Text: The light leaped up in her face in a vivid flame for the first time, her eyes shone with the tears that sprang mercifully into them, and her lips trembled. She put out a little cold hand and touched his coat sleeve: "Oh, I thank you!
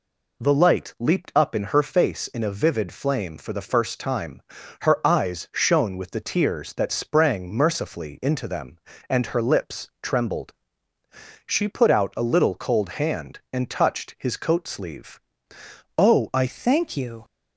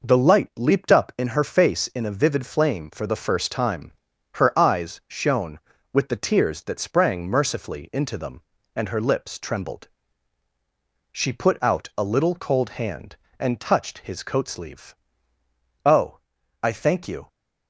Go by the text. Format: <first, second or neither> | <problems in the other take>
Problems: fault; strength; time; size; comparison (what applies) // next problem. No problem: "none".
second | changes voice at "thank"; from 16.4 s on; 0.8 s long